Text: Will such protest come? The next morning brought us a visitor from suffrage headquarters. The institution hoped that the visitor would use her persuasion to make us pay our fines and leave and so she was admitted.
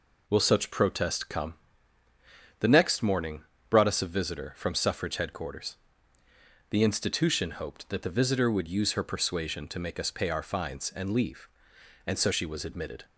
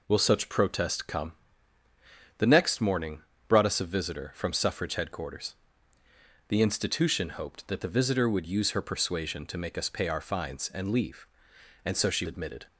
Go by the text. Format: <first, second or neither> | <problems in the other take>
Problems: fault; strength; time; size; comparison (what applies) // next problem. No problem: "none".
first | pauses between "morning" and "brought"; slight; at 3.2 s; 0.26 s long; slight in the first // skips "was"; at 12.2 s